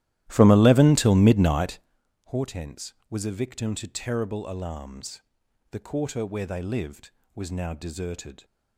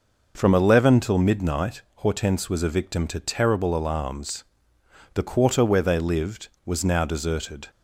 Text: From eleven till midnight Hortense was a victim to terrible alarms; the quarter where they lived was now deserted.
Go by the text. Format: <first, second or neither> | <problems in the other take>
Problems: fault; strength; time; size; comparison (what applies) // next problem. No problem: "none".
second | starts louder than the rest; strong; until 2.0 s; 14.5 dB // pauses between "midnight" and "Hortense"; noticeable; at 1.7 s; 0.46 s long; slight in the second